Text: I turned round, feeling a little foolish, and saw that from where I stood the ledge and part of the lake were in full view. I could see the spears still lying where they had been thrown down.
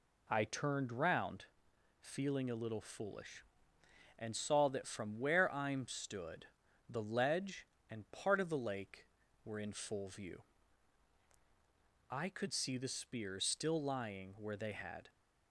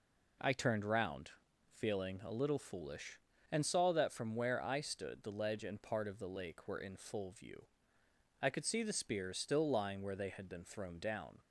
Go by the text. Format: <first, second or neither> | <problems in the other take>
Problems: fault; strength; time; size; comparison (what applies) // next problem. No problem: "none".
second | pauses between "stood" and "the"; at 6.4 s; 0.44 s long // stops before "been thrown down"; at 15.0 s